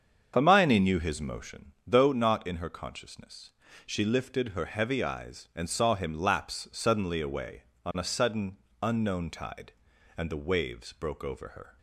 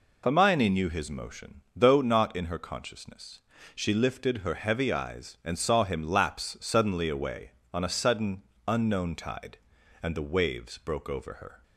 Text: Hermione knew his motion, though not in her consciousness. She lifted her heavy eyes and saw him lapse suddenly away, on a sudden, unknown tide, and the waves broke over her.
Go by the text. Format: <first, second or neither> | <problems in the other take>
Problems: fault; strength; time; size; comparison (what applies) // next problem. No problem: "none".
second | starts louder than the rest; strong; until 1.7 s; 7 dB